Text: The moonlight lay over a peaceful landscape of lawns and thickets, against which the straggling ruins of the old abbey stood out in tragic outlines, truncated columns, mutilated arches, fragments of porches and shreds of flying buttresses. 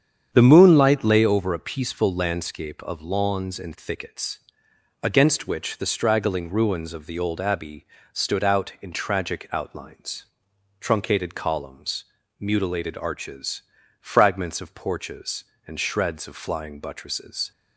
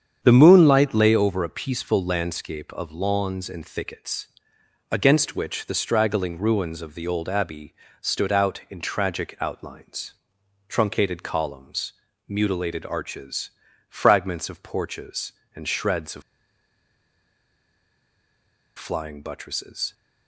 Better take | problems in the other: first | starts louder than the rest; strong; until 1.2 s; 8 dB; strong in the first // pauses between "abbey" and "stood"; slight; at 7.7 s; 0.28 s long; slight in the first // pauses between "of" and "flying"; strong; at 16.2 s; 2.5 s long

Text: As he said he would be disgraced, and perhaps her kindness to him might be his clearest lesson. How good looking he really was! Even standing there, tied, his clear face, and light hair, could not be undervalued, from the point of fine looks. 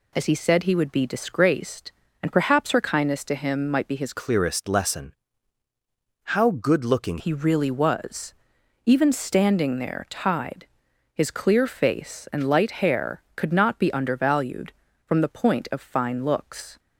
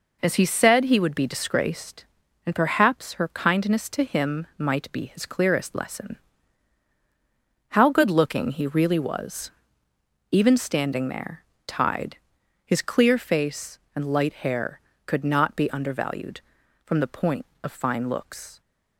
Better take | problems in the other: second | changes voice from "clearest" to "looking"; from 4.1 to 7.1 s; 3.0 s long

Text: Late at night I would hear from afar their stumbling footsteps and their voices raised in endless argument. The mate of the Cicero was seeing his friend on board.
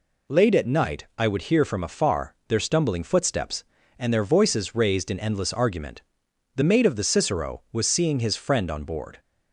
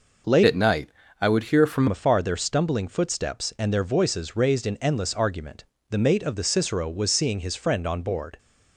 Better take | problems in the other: first | changes voice from "at" to "from"; from 0.4 to 1.8 s; 1.4 s long // pauses between "night" and "I"; slight; at 0.8 s; 0.32 s long

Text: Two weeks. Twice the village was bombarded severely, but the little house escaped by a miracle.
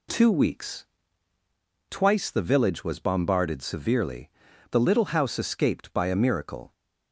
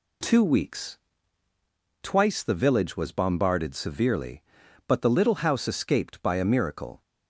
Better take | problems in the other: second | skips "but"; at 4.5 s

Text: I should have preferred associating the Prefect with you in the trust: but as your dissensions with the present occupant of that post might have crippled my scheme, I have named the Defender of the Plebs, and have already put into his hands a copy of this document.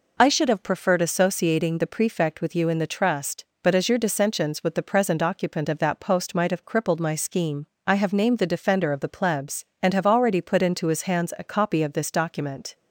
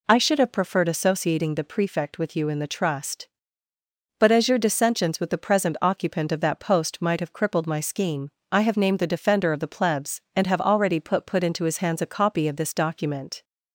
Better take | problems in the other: first | says "put" twice; at 11.2 s

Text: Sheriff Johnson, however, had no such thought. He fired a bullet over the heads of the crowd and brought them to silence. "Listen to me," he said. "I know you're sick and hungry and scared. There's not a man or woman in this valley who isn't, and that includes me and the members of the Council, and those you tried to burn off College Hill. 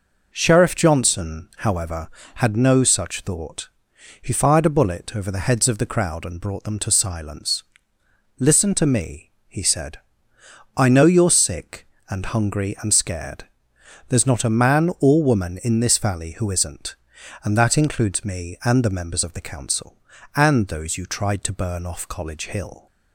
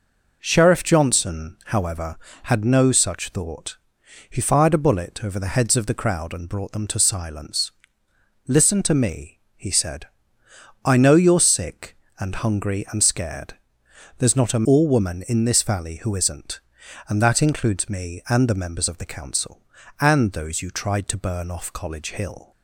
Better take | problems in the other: first | skips "man"; at 14.6 s

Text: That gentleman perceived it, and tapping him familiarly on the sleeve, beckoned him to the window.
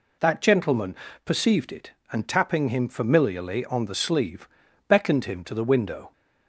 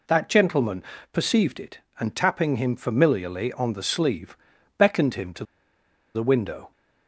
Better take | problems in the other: first | pauses between "gentleman" and "perceived"; slight; at 0.8 s; 0.32 s long; slight in the first // pauses between "to" and "the"; noticeable; at 5.4 s; 0.71 s long

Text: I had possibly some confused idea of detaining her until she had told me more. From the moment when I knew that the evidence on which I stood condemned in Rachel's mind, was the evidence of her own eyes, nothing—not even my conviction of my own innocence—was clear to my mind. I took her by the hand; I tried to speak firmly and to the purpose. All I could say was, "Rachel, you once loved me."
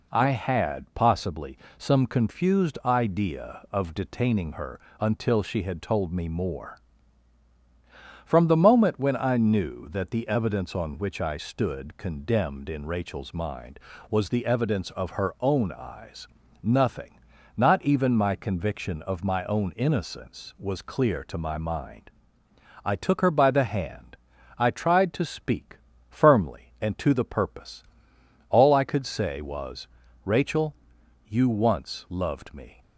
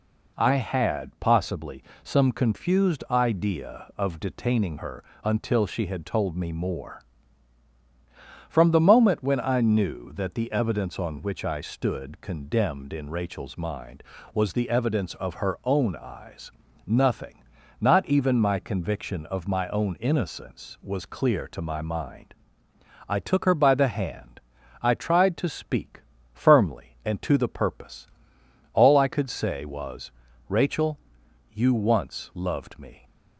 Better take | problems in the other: neither | pauses between "possibly" and "some"; slight; the same in both // pauses between "her" and "until"; slight; the same in both // pauses between "speak" and "firmly"; slight; the same in both

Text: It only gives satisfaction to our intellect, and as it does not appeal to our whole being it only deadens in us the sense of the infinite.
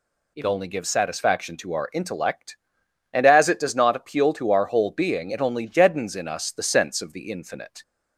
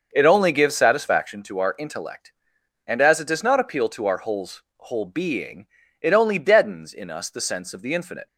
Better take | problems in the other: first | starts louder than the rest; noticeable; until 1.1 s; 6 dB // says "whole" twice; at 4.8 s // pauses between "being" and "it"; slight; at 5.6 s; 0.34 s long

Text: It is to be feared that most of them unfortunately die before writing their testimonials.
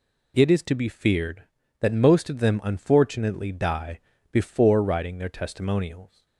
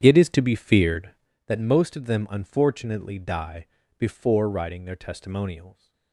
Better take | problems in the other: first | starts louder than the rest; strong; until 1.4 s; 9.5 dB // pauses between "die" and "before"; slight; at 3.6 s; 0.32 s long; slight in the first

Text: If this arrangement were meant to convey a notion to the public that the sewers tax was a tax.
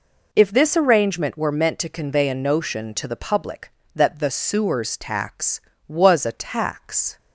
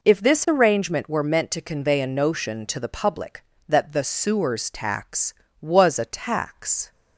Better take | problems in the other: neither | none

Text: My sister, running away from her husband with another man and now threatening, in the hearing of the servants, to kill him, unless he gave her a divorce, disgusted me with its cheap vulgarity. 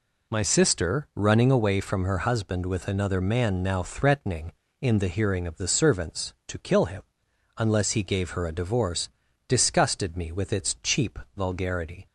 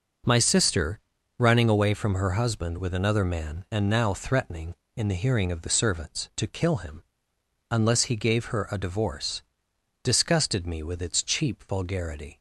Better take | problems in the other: second | skips "and"; at 3.6 s // pauses between "cheap" and "vulgarity"; slight; at 11.1 s; 0.18 s long

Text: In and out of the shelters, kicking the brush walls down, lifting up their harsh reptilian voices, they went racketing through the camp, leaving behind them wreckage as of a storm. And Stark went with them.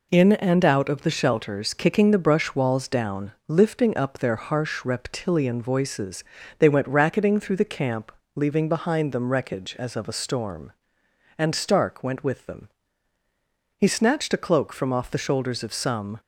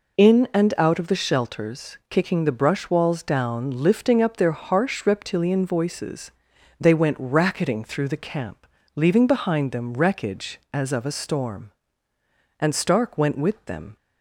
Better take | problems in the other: second | goes on to say "He snatched a cloak from off the shoulders of some"; strong; from 13.7 s on; 2.4 s long

